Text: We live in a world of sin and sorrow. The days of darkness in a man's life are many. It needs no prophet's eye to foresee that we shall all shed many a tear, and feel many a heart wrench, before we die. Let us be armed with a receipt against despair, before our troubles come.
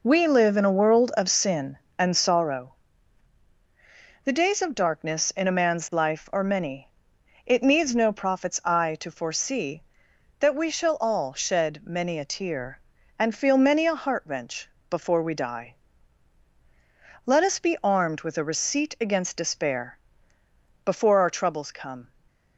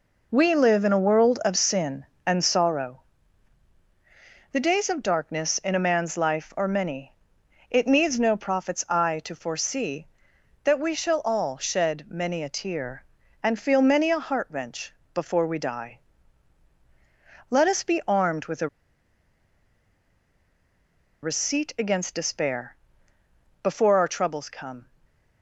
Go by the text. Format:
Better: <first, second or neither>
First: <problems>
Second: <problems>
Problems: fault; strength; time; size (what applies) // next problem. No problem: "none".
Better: first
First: none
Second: pauses between "a" and "receipt"; strong; at 18.6 s; 2.5 s long